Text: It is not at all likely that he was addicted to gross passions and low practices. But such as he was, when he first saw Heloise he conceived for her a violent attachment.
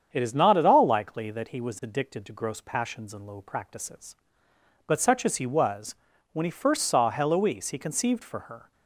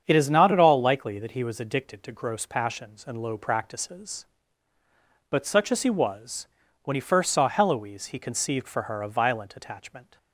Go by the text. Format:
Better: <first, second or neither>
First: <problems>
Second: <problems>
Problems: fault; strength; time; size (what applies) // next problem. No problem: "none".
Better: second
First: starts louder than the rest; strong; until 1.1 s; 8 dB // stops before "a violent attachment"; at 8.7 s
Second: starts louder than the rest; strong; until 1.0 s; 7.5 dB